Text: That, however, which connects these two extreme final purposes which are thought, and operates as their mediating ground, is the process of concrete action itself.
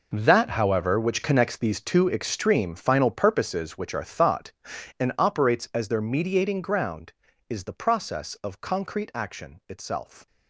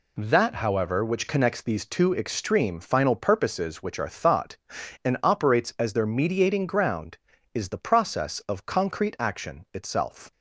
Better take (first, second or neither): second